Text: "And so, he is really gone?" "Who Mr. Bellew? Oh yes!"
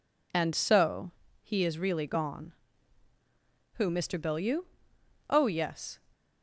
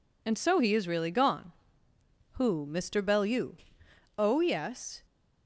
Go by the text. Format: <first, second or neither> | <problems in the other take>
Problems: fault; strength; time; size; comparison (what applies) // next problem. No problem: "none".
neither | none